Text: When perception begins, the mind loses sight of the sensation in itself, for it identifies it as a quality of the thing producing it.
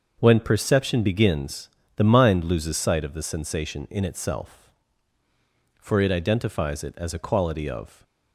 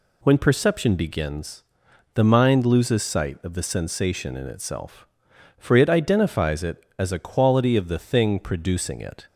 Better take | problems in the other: second | starts louder than the rest; until 1.2 s; 6.5 dB // stops before "the thing producing it"; at 8.0 s

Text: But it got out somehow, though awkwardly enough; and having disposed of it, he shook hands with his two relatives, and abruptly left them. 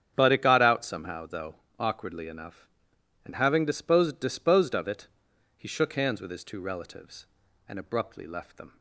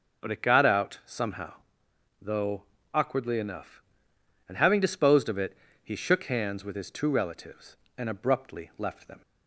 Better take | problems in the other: second | starts louder than the rest; strong; until 1.1 s; 8.5 dB // pauses between "though" and "awkwardly"; slight; at 1.5 s; 0.22 s long; slight in the second // says "disposed" twice; at 4.2 s

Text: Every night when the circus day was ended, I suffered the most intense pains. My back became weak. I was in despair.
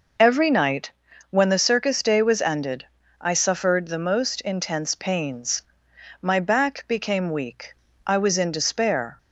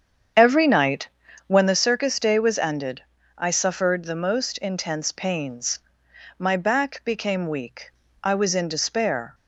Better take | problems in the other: first | starts louder than the rest; strong; until 1.8 s; 8 dB // pauses between "night" and "when"; at 1.0 s; 0.40 s long; also in the first

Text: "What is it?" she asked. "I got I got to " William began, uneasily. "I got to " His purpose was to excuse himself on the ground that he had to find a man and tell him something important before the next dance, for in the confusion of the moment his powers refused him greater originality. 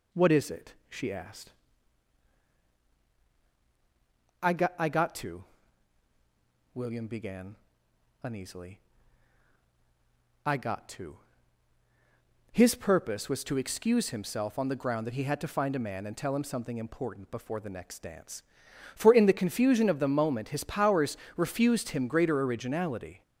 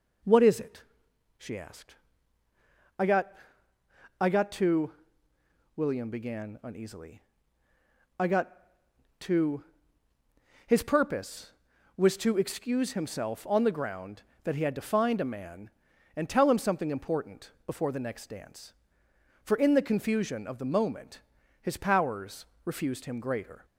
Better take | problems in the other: first | pauses between "got" and "I"; noticeable; at 3.3 s; 0.88 s long // pauses between "moment" and "his"; at 21.1 s; 0.42 s long // pauses between "powers" and "refused"; slight; at 22.4 s; 0.18 s long; slight in the first // stops before "originality"; at 23.6 s

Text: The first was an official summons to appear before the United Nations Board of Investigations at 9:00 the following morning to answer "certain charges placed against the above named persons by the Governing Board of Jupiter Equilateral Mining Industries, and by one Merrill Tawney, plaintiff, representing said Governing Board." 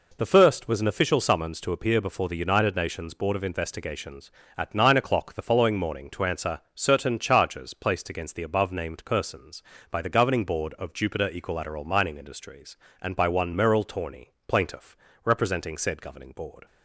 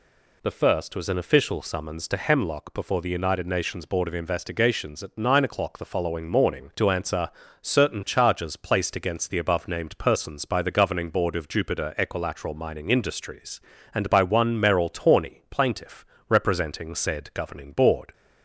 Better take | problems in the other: first | says "hemlock" for "appear"; at 2.1 s // pauses between "answer" and "certain"; slight; at 7.2 s; 0.32 s long

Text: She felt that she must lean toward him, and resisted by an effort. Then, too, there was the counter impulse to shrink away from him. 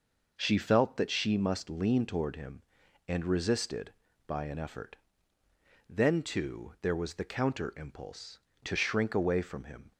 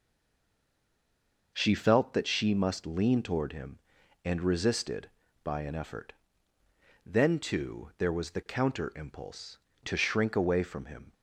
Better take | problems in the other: first | stays silent before the first word; noticeable; until 1.5 s; 1.5 s long

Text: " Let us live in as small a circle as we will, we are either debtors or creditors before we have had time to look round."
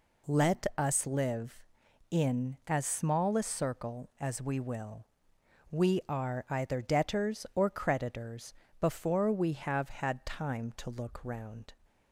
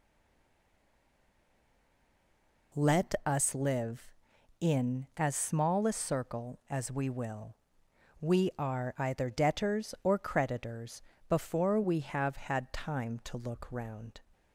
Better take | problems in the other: first | stays silent before the first word; strong; until 2.7 s; 2.7 s long // pauses between "creditors" and "before"; slight; at 11.0 s; 0.26 s long; slight in the first

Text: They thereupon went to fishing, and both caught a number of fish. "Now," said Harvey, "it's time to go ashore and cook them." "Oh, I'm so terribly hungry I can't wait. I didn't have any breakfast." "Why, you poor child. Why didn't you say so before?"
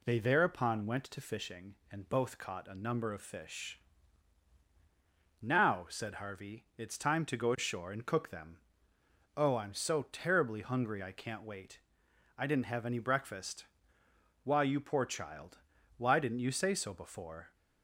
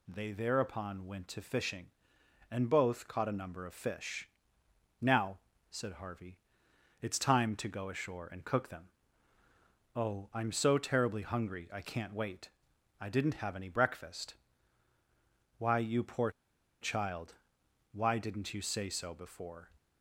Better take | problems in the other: first | pauses between "poor" and "child"; noticeable; at 16.2 s; 0.51 s long

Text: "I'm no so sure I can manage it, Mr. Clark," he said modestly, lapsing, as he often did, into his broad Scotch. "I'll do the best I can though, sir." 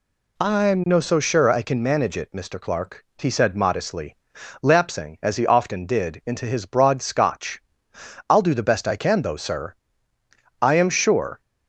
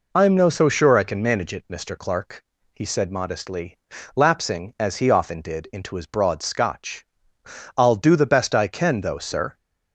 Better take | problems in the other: second | goes on to say "I am sure"; noticeable; from 10.6 s on; 0.78 s long

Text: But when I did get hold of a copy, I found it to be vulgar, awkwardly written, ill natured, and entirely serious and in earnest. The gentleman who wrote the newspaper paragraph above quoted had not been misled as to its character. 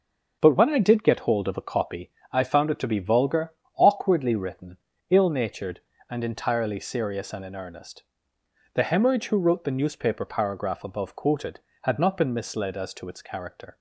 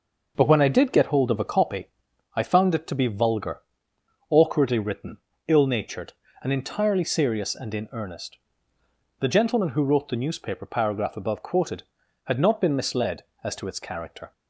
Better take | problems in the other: second | says "hemorrhage" for "gentleman"; at 8.8 s

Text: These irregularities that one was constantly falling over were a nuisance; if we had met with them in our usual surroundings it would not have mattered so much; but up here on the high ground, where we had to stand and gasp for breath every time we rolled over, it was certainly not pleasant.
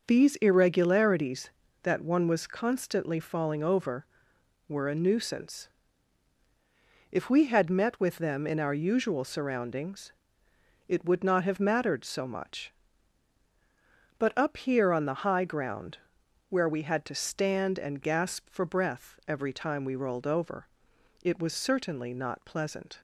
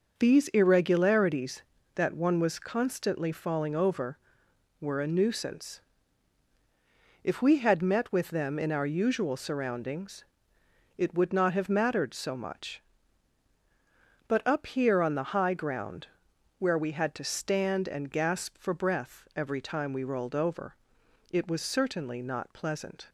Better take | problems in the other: neither | pauses between "surroundings" and "it"; noticeable; the same in both

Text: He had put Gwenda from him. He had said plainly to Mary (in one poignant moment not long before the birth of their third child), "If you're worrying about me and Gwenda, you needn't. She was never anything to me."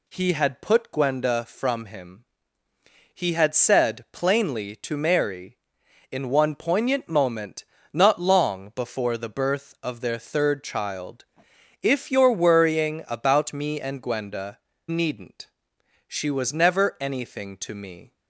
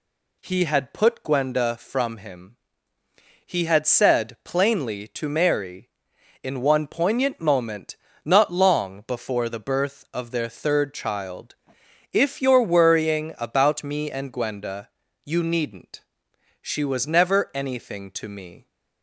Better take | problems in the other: second | pauses between "moment" and "not"; slight; at 7.6 s; 0.26 s long; slight in the second // skips "you"; at 14.7 s

